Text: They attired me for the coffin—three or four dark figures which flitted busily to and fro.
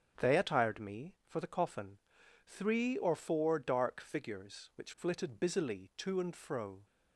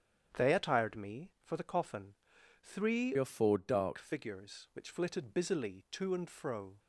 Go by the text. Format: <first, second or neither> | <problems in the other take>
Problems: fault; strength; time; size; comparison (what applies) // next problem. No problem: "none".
first | starts louder than the rest; strong; until 1.4 s; 8.5 dB; strong in the first // changes voice from "or" to "dark"; from 3.1 to 3.9 s; 0.8 s long